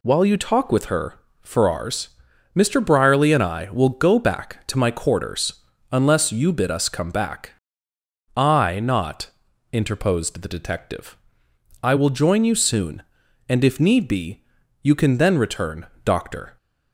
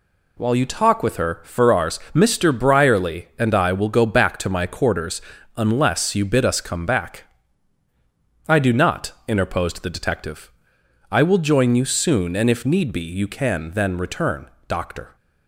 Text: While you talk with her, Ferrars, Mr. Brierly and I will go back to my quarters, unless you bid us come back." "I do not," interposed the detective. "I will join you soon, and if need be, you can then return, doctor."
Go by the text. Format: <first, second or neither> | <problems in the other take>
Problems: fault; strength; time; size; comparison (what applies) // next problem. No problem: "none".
second | skips "do"; at 8.7 s